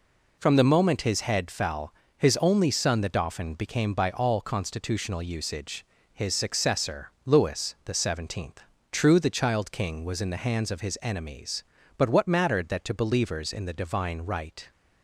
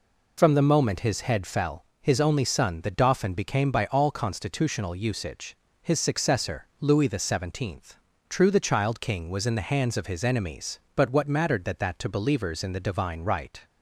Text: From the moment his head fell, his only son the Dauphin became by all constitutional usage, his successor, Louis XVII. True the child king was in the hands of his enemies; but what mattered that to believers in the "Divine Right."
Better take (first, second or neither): first